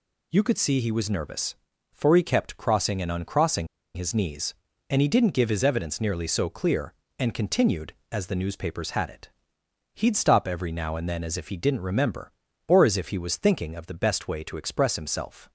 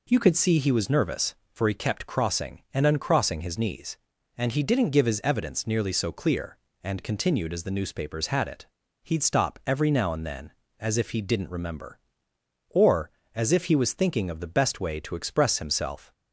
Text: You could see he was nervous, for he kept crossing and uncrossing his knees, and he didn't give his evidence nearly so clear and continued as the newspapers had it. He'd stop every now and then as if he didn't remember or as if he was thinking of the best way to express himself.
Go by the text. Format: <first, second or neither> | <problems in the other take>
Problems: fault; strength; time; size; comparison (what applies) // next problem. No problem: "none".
second | pauses between "uncrossing" and "his"; slight; at 3.6 s; 0.29 s long